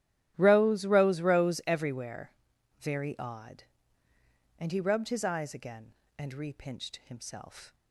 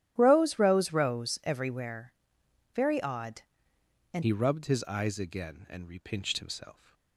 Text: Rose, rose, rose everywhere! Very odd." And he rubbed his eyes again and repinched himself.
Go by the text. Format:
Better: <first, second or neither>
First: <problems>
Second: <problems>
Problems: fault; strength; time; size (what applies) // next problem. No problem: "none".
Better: first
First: starts louder than the rest; strong; until 1.3 s; 12.5 dB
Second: starts louder than the rest; strong; until 1.1 s; 12.5 dB // changes voice at "he"; from 4.2 s on; 2.7 s long